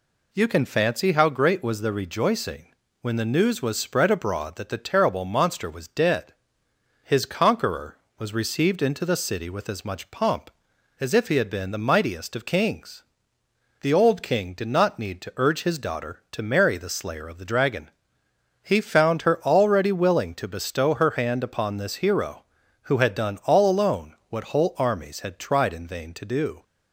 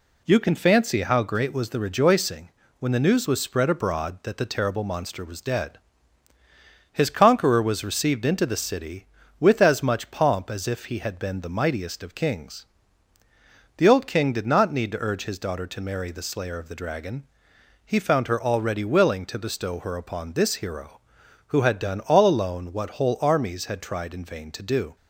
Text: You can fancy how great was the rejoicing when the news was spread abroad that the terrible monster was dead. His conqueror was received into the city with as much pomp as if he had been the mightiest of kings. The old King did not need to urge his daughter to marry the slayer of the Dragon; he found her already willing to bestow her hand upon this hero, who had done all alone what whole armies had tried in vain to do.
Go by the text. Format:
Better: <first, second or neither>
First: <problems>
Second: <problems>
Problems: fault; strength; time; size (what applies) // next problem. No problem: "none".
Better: first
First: pauses between "rejoicing" and "when"; slight; at 2.6 s; 0.34 s long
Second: pauses between "rejoicing" and "when"; slight; at 2.4 s; 0.30 s long // skips "hand"; at 19.9 s